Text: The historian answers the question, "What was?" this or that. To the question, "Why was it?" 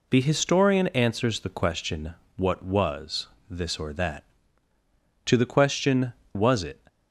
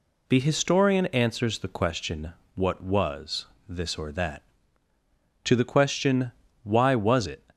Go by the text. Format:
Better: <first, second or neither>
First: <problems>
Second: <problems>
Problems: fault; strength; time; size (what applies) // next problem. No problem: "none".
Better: second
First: skips "Why"; at 6.2 s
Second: none